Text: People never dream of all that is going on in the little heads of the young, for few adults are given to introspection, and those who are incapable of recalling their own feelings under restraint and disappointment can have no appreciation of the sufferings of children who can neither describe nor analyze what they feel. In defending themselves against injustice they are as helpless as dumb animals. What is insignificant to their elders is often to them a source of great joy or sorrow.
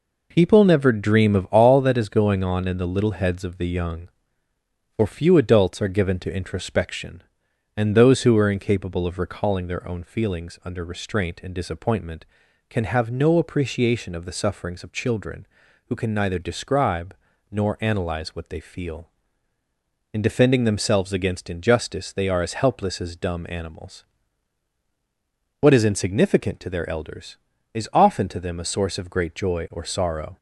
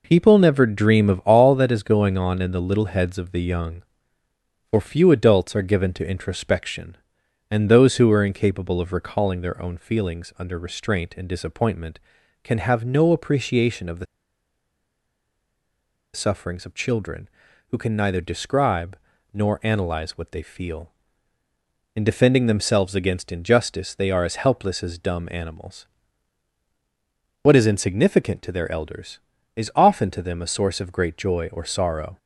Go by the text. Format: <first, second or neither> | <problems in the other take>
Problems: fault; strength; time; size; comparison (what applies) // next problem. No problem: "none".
first | pauses between "the" and "sufferings"; strong; at 14.0 s; 2.0 s long // pauses between "describe" and "nor"; at 18.9 s; 0.38 s long; also in the first